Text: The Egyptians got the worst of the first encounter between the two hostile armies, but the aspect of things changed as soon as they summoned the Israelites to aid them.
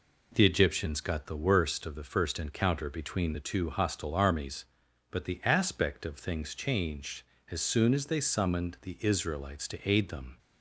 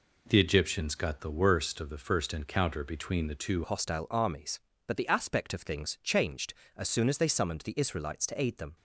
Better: first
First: none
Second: changes voice at "hostile"; from 3.6 s on; 5.1 s long

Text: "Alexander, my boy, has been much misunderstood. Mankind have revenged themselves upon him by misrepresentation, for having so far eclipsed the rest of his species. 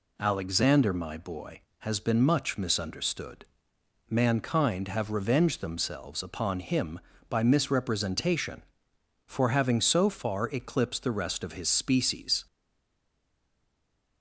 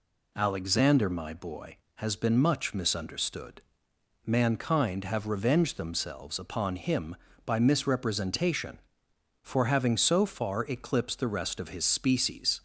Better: second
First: stays silent after the last word; noticeable; from 12.4 s on; 1.8 s long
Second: none

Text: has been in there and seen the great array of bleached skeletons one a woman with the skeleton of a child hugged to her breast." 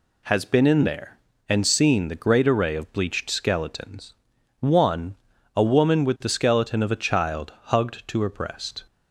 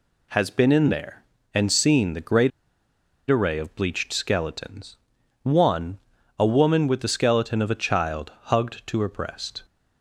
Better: first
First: pauses between "skeletons" and "one"; noticeable; at 4.1 s; 0.46 s long // pauses between "one" and "a"; at 5.1 s; 0.42 s long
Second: pauses between "great" and "array"; noticeable; at 2.5 s; 0.80 s long // pauses between "skeletons" and "one"; noticeable; at 4.9 s; 0.46 s long // pauses between "one" and "a"; at 5.9 s; 0.42 s long

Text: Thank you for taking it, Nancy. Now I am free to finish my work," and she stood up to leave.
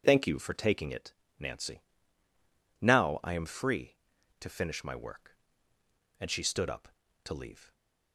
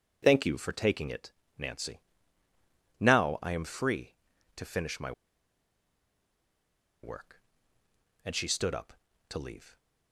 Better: first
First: none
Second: pauses between "my" and "work"; strong; at 5.1 s; 1.9 s long

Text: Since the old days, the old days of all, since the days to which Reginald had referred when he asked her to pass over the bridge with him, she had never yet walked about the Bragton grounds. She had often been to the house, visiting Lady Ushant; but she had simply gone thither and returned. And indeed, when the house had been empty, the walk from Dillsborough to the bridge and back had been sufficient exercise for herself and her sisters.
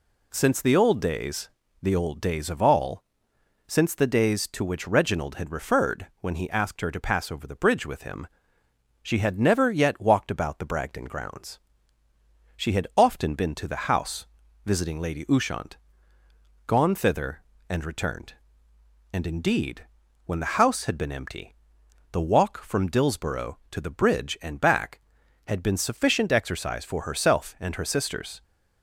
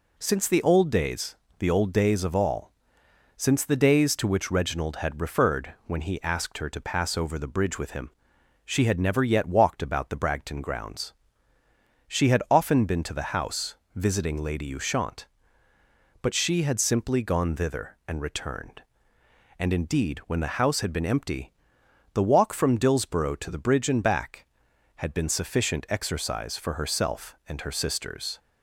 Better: second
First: skips "but she had simply"; at 16.2 s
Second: none

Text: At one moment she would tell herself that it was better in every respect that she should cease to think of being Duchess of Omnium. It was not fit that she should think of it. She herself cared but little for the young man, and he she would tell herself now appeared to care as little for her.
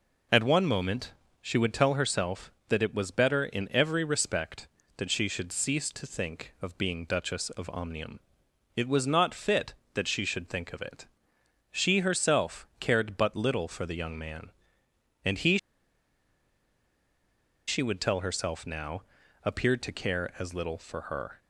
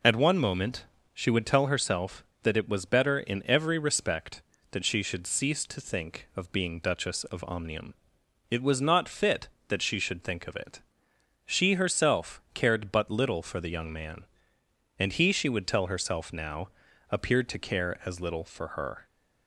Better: second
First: pauses between "moment" and "she"; slight; at 1.1 s; 0.28 s long // pauses between "he" and "she"; strong; at 15.5 s; 2.1 s long // pauses between "now" and "appeared"; at 19.0 s; 0.42 s long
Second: pauses between "moment" and "she"; slight; at 0.8 s; 0.28 s long // pauses between "now" and "appeared"; at 16.6 s; 0.42 s long

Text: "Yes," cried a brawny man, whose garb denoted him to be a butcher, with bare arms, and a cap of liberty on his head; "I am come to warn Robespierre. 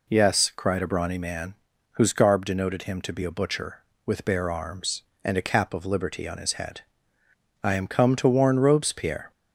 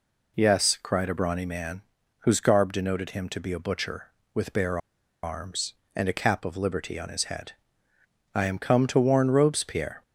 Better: first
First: none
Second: pauses between "bare" and "arms"; at 4.7 s; 0.44 s long

